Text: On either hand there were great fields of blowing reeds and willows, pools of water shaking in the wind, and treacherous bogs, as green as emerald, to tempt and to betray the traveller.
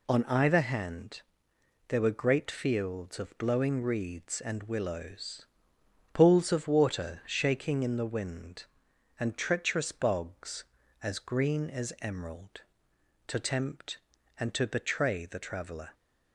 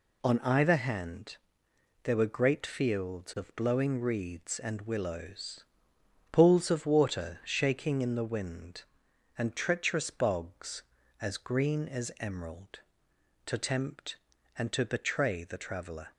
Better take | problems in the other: neither | pauses between "hand" and "there"; noticeable; the same in both

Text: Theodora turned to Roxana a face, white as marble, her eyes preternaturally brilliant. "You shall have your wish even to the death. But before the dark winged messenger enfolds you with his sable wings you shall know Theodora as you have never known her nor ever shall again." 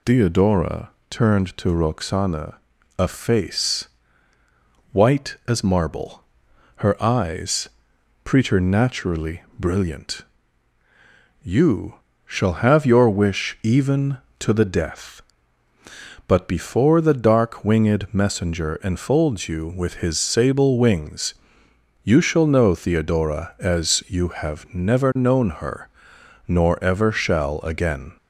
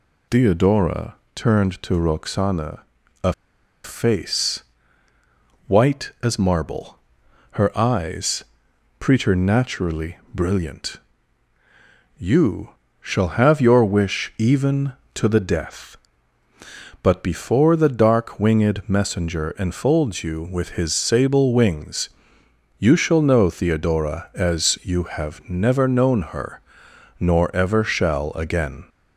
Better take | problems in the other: first | pauses between "Theodora" and "turned"; slight; at 1.1 s; 0.20 s long; slight in the first // pauses between "Roxana" and "a"; at 2.8 s; 0.42 s long; also in the first // pauses between "a" and "face"; noticeable; at 3.3 s; 0.51 s long // pauses between "eyes" and "preternaturally"; noticeable; at 8.4 s; 0.56 s long; noticeable in the first // pauses between "You" and "shall"; slight; at 12.6 s; 0.32 s long; slight in the first // pauses between "wings" and "you"; noticeable; at 22.0 s; 0.70 s long; noticeable in the first // pauses between "her" and "nor"; noticeable; at 26.6 s; 0.58 s long; noticeable in the first

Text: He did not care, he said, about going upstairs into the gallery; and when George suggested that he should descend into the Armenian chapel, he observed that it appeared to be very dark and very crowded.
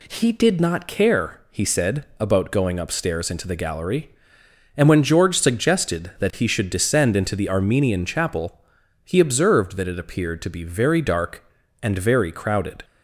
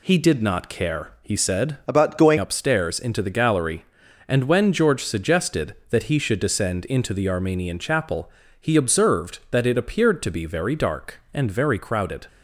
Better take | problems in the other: first | changes voice from "about" to "going"; from 1.8 to 2.3 s; 0.5 s long

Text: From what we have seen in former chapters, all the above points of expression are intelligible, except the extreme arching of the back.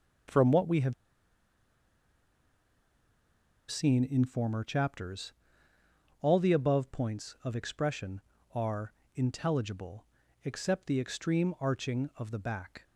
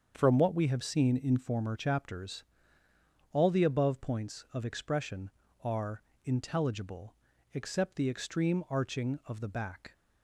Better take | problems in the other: second | starts louder than the rest; until 4.0 s; 7 dB; also in the second // pauses between "have" and "seen"; strong; at 0.9 s; 2.7 s long // pauses between "are" and "intelligible"; slight; at 8.9 s; 0.20 s long; slight in the second

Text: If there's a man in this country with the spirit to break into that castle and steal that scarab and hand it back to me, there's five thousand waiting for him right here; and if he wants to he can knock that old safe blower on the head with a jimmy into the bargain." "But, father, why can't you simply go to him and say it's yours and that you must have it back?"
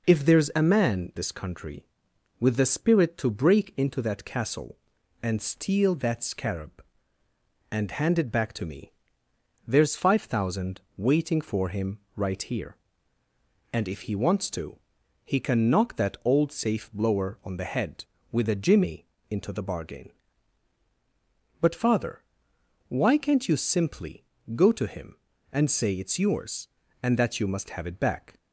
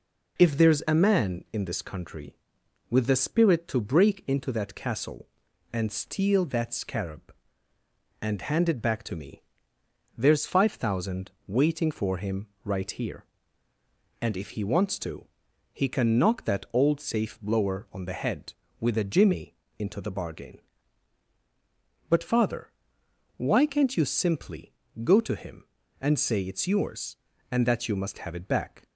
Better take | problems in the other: second | skips "in"; at 1.1 s // pauses between "thousand" and "waiting"; slight; at 10.7 s; 0.16 s long; slight in the second // pauses between "him" and "right"; slight; at 11.9 s; 0.18 s long; slight in the second // pauses between "to" and "he"; noticeable; at 14.7 s; 0.48 s long; noticeable in the second // pauses between "jimmy" and "into"; slight; at 19.0 s; 0.24 s long; slight in the second // pauses between "simply" and "go"; slight; at 24.2 s; 0.32 s long; slight in the second

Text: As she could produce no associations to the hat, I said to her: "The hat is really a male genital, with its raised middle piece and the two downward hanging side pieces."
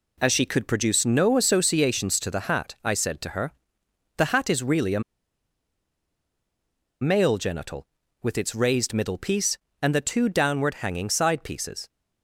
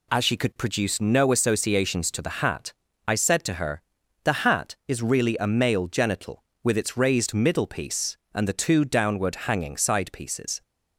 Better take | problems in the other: second | pauses between "a" and "male"; strong; at 5.0 s; 2.0 s long

